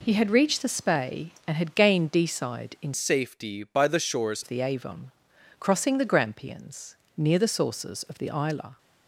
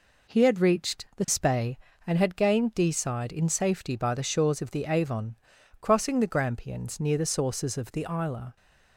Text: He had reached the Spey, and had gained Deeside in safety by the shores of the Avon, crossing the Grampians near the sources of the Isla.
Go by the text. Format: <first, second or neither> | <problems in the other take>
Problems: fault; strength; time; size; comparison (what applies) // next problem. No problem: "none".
second | changes voice from "safety" to "shores"; from 2.9 to 4.4 s; 1.5 s long // pauses between "Grampians" and "near"; slight; at 6.9 s; 0.20 s long